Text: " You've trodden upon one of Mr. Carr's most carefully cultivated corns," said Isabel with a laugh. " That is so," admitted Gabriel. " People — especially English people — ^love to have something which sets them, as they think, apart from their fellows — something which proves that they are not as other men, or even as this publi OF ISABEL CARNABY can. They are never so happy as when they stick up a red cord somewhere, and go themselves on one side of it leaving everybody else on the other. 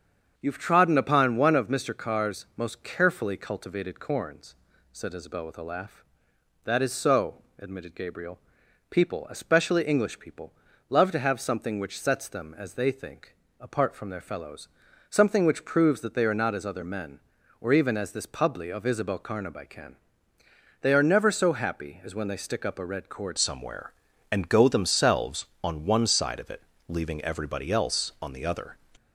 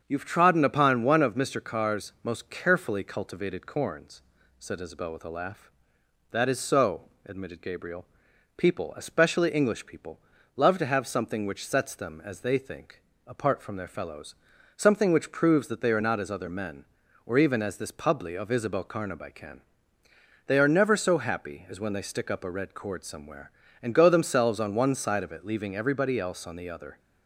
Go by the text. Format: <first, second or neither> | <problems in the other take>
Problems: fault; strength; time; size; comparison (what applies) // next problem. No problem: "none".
second | starts louder than the rest; strong; until 1.3 s; 8 dB; strong in the second // changes voice at "somewhere"; from 23.3 s on; 5.4 s long // pauses between "it" and "leaving"; slight; at 26.6 s; 0.24 s long